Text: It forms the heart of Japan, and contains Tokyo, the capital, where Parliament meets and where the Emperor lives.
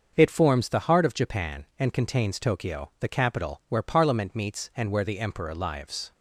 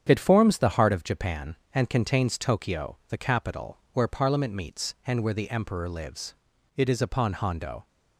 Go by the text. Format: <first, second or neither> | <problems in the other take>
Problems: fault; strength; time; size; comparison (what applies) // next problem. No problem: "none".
first | starts louder than the rest; strong; until 1.0 s; 8.5 dB; also in the first // goes on to say "It is upon Hondo"; noticeable; from 6.7 s on; 1.1 s long